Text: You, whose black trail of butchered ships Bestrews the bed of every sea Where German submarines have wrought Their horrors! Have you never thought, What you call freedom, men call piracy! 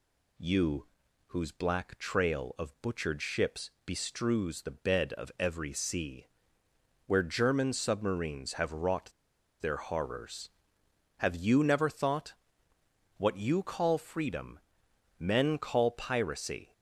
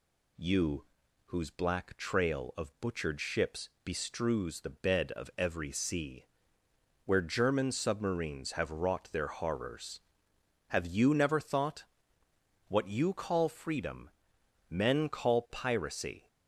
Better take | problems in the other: second | pauses between "ships" and "Bestrews"; slight; at 3.7 s; 0.16 s long; slight in the second // pauses between "sea" and "Where"; noticeable; at 6.2 s; 0.80 s long; noticeable in the second // pauses between "wrought" and "Their"; noticeable; at 9.1 s; 0.50 s long

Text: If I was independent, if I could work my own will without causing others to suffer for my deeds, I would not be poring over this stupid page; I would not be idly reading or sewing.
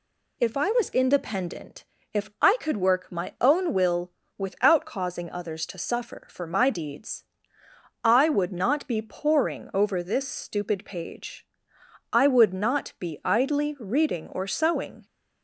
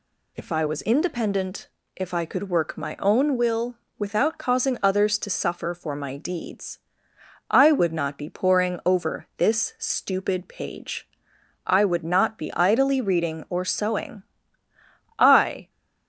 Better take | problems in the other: first | pauses between "will" and "without"; slight; at 3.7 s; 0.22 s long; slight in the first // goes on to say "I"; from 15.1 s on; 0.52 s long

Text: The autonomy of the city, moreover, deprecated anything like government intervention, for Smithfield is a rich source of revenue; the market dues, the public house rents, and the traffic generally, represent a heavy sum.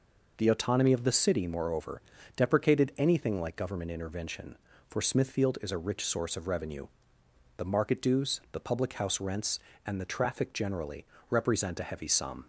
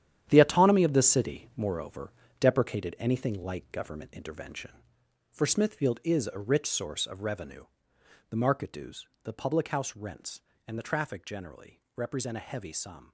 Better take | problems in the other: first | gets quieter; strong; throughout; 10 dB

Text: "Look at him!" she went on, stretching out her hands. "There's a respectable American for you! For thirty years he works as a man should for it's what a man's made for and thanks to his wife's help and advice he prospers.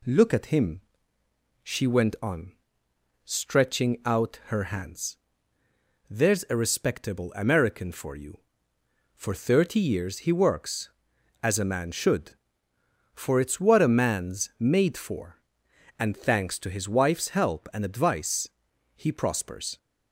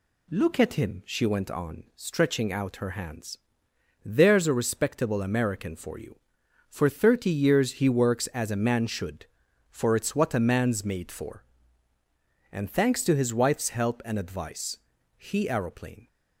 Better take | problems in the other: first | pauses between "advice" and "he"; at 14.7 s; 0.40 s long; noticeable in the first // says "aeroplane" for "prospers"; at 15.4 s

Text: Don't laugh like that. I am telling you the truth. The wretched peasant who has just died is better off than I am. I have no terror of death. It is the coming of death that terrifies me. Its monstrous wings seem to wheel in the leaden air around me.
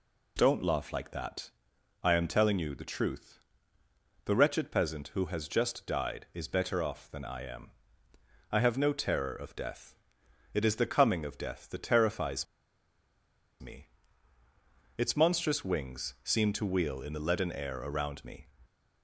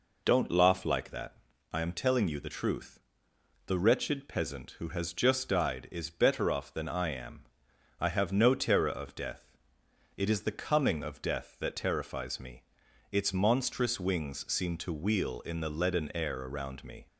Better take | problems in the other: second | pauses between "terrifies" and "me"; at 12.4 s; 1.1 s long

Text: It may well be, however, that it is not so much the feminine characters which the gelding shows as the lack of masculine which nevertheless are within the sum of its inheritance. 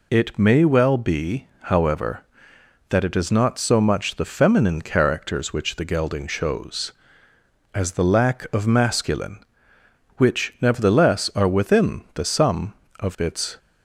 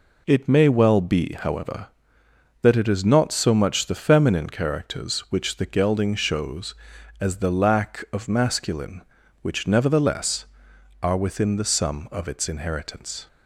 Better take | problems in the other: second | stops before "inheritance"; at 13.5 s

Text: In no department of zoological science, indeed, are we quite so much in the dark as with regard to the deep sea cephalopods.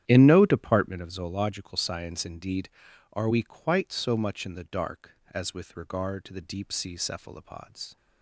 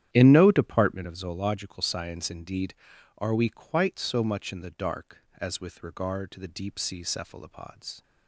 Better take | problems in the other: neither | starts louder than the rest; strong; the same in both

